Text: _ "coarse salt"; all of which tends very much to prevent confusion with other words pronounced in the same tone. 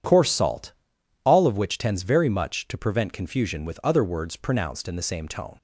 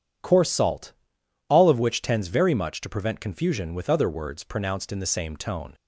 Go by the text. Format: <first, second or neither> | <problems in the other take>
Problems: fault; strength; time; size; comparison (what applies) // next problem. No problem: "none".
neither | none